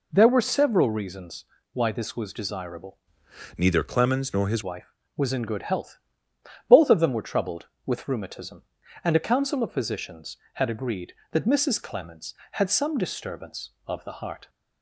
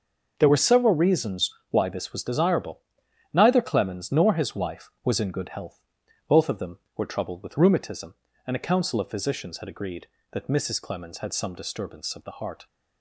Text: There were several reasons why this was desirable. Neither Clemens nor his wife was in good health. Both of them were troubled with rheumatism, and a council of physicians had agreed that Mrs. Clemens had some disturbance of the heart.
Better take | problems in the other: second | pauses between "reasons" and "why"; slight; at 1.4 s; 0.28 s long; slight in the second // changes voice from "Neither" to "his"; from 3.5 to 4.6 s; 1.1 s long

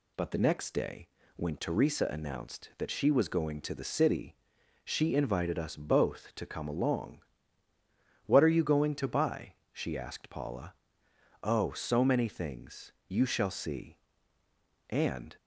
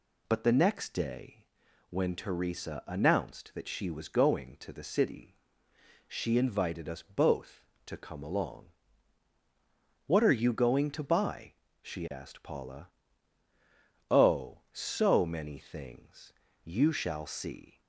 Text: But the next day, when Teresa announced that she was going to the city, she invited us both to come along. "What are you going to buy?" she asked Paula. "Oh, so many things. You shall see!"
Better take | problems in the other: second | goes on to say "And"; slight; from 14.8 s on; 0.48 s long

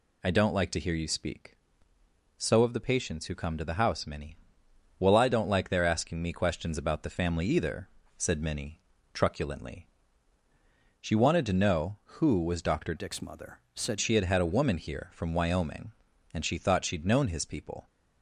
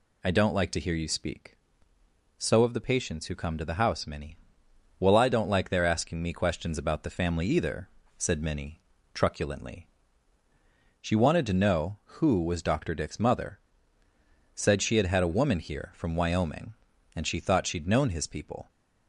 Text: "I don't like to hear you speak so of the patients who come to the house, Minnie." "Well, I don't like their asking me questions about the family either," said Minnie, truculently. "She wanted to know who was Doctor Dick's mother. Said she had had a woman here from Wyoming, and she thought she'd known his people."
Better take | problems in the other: second | changes voice from "Dick's" to "Said"; from 12.9 to 13.9 s; 1.0 s long

